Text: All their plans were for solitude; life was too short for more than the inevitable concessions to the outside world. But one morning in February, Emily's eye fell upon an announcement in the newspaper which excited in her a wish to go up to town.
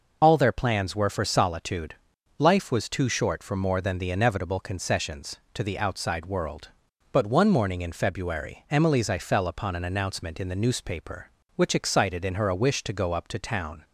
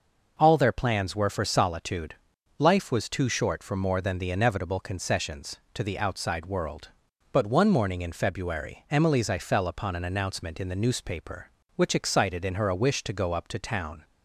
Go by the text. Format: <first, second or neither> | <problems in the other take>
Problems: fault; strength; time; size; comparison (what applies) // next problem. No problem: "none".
second | loses the start of "All"; at 0.2 s; 35 ms